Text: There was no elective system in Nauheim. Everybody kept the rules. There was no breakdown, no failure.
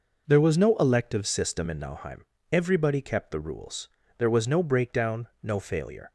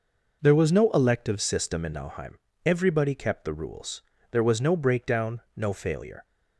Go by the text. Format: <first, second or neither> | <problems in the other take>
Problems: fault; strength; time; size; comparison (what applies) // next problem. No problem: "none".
neither | none